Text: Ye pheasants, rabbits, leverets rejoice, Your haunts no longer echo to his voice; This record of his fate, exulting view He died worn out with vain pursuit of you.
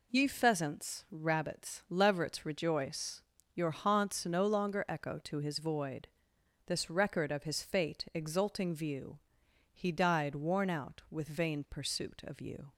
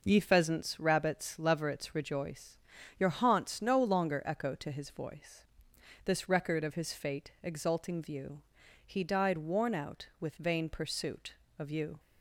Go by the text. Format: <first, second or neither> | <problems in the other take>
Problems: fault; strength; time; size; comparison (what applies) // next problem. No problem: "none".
second | says "void" for "voice"; at 5.5 s // pauses between "view" and "He"; noticeable; at 9.1 s; 0.52 s long; noticeable in the second